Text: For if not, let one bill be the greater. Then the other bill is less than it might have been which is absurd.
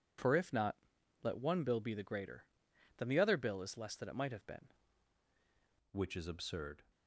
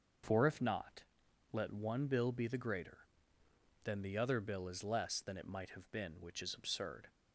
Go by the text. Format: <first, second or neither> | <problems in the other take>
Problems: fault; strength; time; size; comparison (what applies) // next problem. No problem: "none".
second | changes voice at "which"; from 5.9 s on; 0.9 s long